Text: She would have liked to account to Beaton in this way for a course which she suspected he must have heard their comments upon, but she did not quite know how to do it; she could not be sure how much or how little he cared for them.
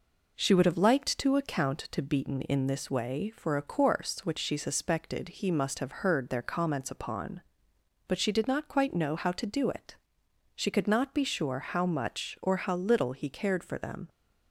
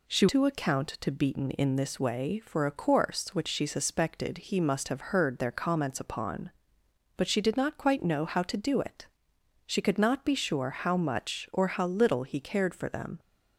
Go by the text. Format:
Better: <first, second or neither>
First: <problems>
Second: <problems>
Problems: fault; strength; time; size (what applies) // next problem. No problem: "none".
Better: first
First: none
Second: skips "would have liked"; at 0.2 s